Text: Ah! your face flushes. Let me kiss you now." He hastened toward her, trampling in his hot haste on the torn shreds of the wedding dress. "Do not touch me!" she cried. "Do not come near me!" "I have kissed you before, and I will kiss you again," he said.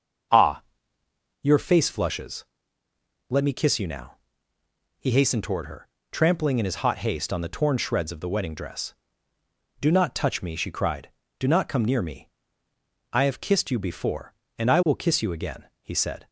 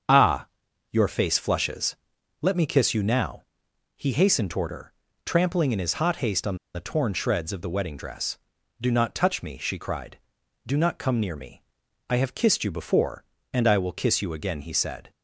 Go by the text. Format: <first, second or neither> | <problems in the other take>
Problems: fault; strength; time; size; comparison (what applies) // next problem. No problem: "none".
first | starts louder than the rest; strong; until 1.5 s; 7 dB; also in the first // pauses between "on" and "the"; slight; at 6.5 s; 0.16 s long